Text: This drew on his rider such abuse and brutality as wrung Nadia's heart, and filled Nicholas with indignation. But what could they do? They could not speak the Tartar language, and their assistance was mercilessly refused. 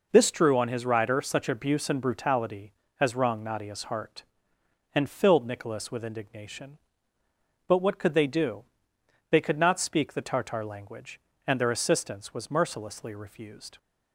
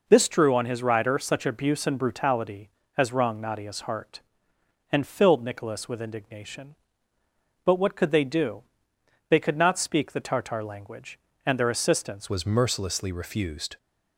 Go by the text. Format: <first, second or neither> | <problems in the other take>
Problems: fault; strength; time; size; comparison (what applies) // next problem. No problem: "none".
first | changes voice at "was"; from 12.2 s on; 1.5 s long